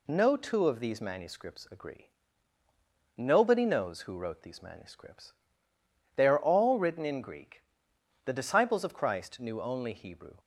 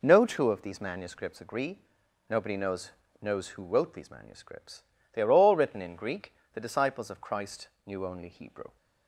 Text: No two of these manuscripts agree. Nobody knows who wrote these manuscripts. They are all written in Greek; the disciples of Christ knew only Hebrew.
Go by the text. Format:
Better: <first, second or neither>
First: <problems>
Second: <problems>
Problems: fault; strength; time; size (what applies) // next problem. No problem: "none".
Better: first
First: none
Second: says "knows" twice; at 3.1 s // pauses between "Christ" and "knew"; slight; at 7.6 s; 0.18 s long